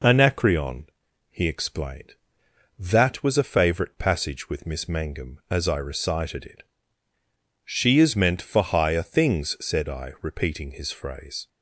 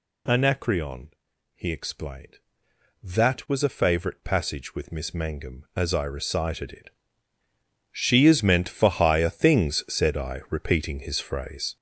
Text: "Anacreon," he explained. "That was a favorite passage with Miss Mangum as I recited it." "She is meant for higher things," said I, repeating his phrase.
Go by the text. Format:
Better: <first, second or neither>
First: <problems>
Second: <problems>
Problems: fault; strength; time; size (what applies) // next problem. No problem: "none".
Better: first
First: none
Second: gets louder; strong; throughout; 8 dB